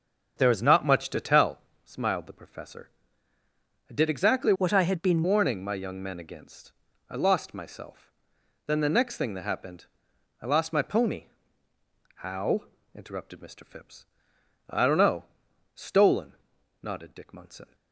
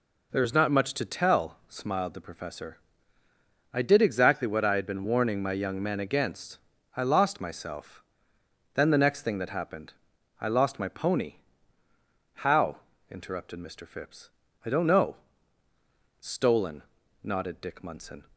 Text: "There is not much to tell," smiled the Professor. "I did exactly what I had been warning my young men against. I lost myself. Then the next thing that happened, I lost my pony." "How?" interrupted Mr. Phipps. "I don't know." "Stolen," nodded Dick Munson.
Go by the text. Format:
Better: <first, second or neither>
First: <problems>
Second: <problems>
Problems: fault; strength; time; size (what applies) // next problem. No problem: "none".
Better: second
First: starts louder than the rest; until 1.4 s; 7 dB // changes voice from "what" to "been"; from 4.5 to 5.2 s; 0.7 s long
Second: none